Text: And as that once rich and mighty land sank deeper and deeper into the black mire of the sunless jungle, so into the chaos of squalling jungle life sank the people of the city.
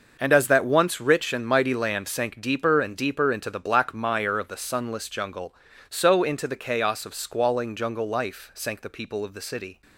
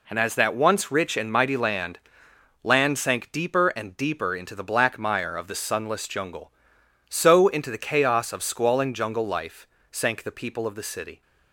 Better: first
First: none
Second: says "land" twice; at 2.6 s // pauses between "life" and "sank"; slight; at 9.6 s; 0.24 s long

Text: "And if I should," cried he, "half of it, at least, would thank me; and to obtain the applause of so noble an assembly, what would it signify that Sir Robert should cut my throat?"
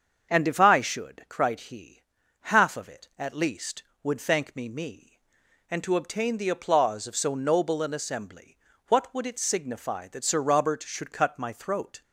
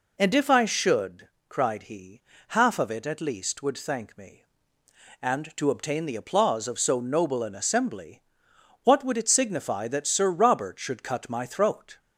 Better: second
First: starts louder than the rest; until 1.3 s; 7 dB // says "me" twice; at 4.6 s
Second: none

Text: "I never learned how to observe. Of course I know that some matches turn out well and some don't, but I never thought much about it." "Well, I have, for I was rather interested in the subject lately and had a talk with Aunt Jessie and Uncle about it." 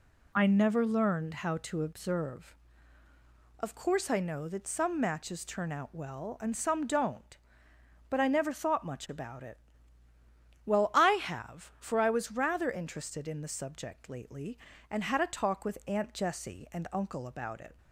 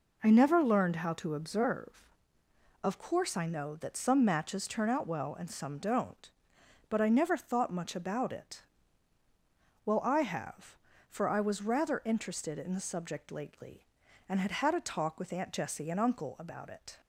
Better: first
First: none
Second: says "had" twice; at 14.5 s

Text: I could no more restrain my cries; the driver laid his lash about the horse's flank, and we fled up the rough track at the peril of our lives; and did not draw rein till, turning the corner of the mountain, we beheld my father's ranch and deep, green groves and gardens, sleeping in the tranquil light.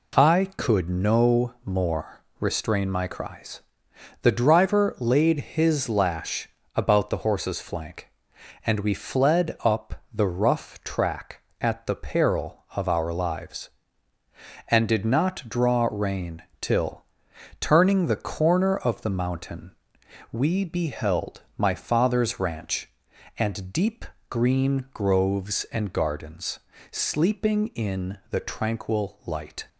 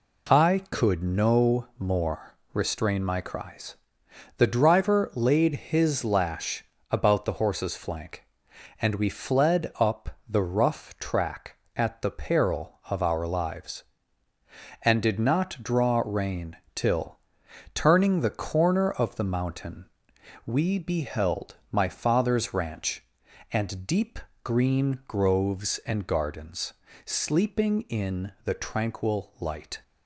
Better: neither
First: pauses between "more" and "restrain"; slight; at 2.2 s; 0.16 s long // pauses between "lash" and "about"; slight; at 6.5 s; 0.26 s long // pauses between "rein" and "till"; slight; at 16.4 s; 0.18 s long // pauses between "beheld" and "my"; slight; at 21.4 s; 0.16 s long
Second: pauses between "more" and "restrain"; slight; at 2.3 s; 0.16 s long // pauses between "lash" and "about"; slight; at 6.6 s; 0.26 s long // pauses between "rein" and "till"; slight; at 16.5 s; 0.18 s long // pauses between "beheld" and "my"; slight; at 21.5 s; 0.16 s long

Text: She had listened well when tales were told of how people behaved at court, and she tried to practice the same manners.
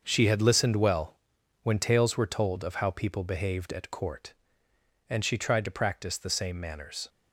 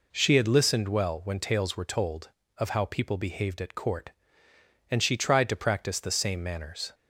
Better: second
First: gets quieter; strong; throughout; 8.5 dB // pauses between "well" and "when"; noticeable; at 1.1 s; 0.46 s long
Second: none

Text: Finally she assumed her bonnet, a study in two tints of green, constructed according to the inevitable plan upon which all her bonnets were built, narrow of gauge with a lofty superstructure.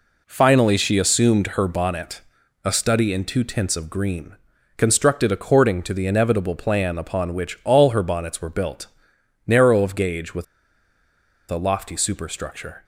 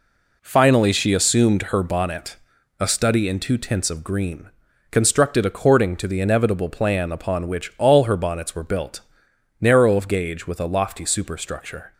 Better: second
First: pauses between "with" and "a"; at 10.4 s; 1.0 s long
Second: none

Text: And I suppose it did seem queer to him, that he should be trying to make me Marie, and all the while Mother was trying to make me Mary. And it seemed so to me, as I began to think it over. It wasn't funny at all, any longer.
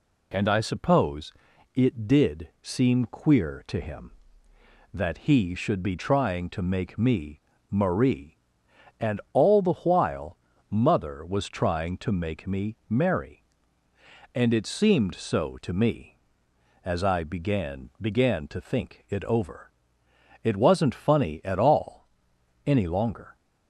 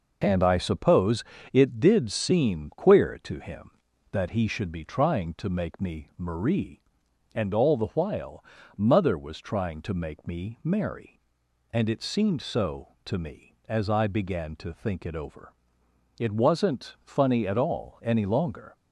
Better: second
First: pauses between "suppose" and "it"; at 1.3 s; 0.44 s long // pauses between "me" and "Marie"; slight; at 7.4 s; 0.30 s long // pauses between "while" and "Mother"; slight; at 10.3 s; 0.32 s long // says "began" twice; at 17.9 s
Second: pauses between "suppose" and "it"; slight; at 1.2 s; 0.28 s long // pauses between "while" and "Mother"; slight; at 8.4 s; 0.32 s long

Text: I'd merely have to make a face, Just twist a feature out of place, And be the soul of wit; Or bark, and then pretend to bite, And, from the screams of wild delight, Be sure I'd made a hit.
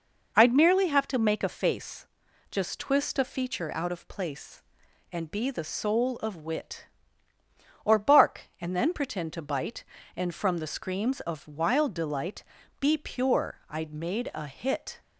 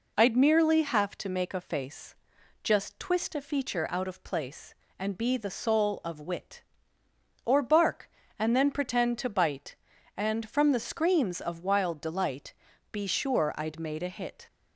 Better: second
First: says "pure" for "sure"; at 12.9 s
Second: none

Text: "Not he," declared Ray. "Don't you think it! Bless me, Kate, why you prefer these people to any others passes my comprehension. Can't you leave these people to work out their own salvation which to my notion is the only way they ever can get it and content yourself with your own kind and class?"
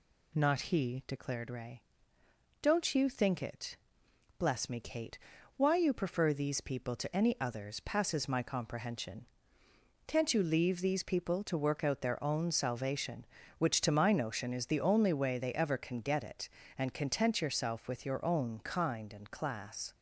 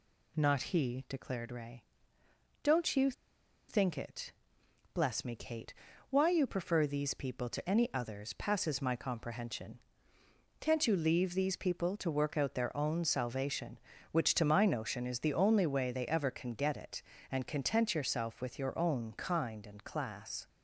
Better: first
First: none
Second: pauses between "you" and "think"; noticeable; at 3.0 s; 0.59 s long

